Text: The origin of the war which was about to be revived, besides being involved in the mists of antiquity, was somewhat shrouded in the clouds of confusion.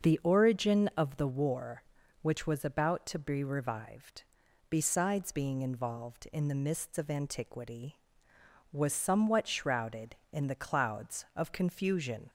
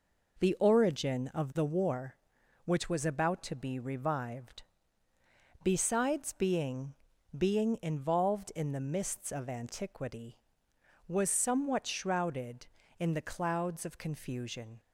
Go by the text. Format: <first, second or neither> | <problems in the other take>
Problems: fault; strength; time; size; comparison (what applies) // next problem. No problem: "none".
first | says "being" twice; at 7.3 s